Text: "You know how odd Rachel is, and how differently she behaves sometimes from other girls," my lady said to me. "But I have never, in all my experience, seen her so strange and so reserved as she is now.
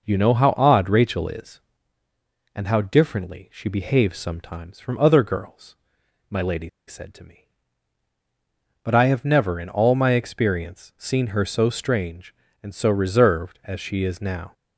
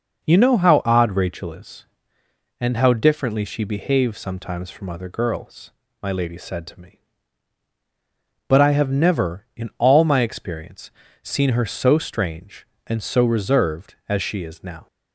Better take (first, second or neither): second